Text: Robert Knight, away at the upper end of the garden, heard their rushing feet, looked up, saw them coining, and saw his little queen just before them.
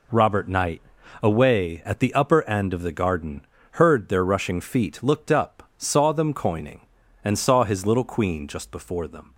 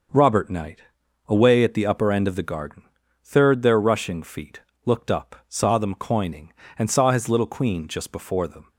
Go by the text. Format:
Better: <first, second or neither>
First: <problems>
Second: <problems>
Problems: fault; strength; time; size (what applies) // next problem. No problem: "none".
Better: first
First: none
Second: starts louder than the rest; until 1.6 s; 6 dB // says "third" for "heard"; at 3.2 s